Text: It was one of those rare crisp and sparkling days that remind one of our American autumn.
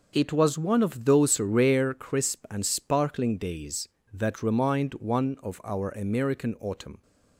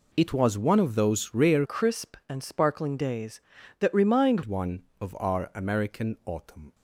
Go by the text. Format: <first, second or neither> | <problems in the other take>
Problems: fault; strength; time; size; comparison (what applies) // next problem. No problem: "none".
first | changes voice from "crisp" to "remind"; from 1.6 to 4.4 s; 2.8 s long